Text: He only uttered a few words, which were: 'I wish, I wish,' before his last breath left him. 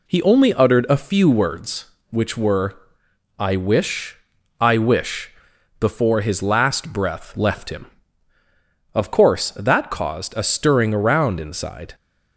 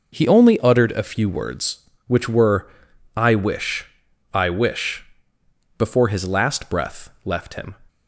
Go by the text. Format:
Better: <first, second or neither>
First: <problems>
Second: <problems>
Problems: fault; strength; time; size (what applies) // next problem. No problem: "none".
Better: second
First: goes on to say "Of course that caused a stirring around inside"; strong; from 8.9 s on; 3.0 s long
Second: none